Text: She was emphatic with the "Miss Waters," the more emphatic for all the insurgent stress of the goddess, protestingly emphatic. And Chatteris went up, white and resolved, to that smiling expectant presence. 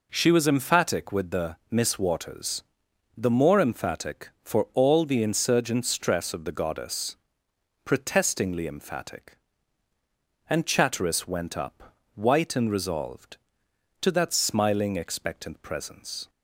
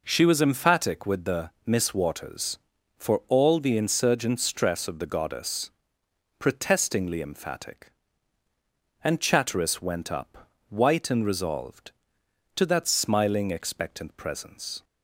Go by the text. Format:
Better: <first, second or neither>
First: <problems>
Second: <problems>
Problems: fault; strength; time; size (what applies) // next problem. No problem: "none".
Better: first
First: none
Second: skips "the more emphatic"; at 2.7 s